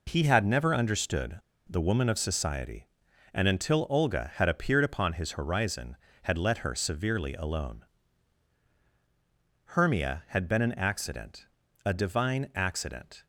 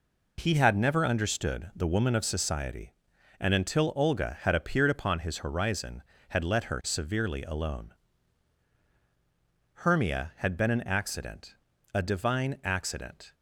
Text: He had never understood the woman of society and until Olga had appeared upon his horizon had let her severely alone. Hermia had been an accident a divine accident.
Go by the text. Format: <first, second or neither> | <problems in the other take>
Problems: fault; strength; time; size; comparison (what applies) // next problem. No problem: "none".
second | pauses between "understood" and "the"; slight; at 1.3 s; 0.30 s long // pauses between "accident" and "a"; at 11.4 s; 0.40 s long; also in the second